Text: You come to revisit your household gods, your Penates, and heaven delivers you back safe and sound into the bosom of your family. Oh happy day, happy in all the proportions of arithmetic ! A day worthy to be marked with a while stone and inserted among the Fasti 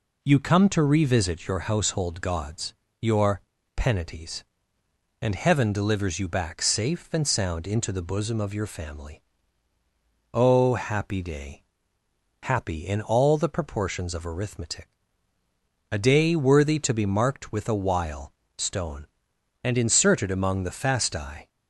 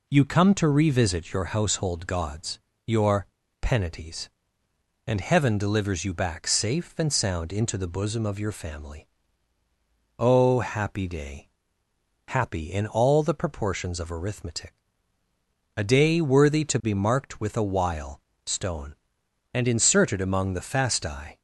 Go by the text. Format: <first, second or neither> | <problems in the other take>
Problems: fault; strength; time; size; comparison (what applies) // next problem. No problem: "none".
neither | pauses between "your" and "Penates"; slight; the same in both // pauses between "while" and "stone"; slight; the same in both